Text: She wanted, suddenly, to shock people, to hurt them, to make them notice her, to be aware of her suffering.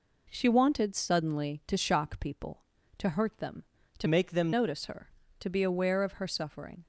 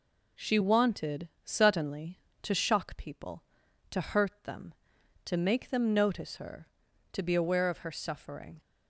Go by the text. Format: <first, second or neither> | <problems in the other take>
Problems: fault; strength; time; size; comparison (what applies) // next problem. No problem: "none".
second | changes voice from "make" to "them"; from 4.0 to 4.5 s; 0.5 s long